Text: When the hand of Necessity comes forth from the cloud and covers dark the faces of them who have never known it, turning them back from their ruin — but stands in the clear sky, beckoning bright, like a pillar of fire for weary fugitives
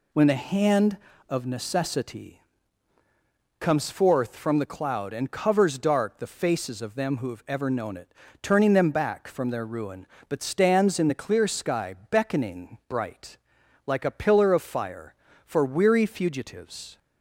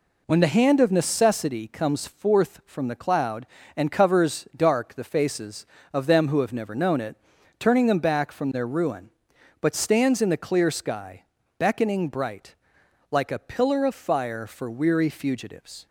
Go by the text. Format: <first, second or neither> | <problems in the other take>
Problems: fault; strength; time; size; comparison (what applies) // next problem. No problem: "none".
second | pauses between "Necessity" and "comes"; at 2.4 s; 1.1 s long // says "ever" for "never"; at 7.4 s